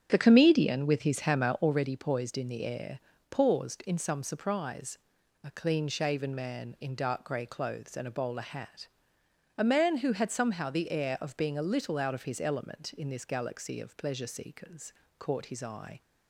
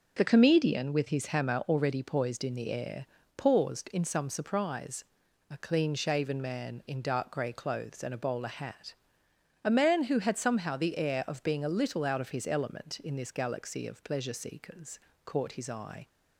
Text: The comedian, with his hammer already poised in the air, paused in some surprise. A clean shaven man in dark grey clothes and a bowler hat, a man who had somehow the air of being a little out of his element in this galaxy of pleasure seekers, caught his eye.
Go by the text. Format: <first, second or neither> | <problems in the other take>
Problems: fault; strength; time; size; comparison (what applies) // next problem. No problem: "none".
second | starts louder than the rest; strong; until 1.8 s; 8.5 dB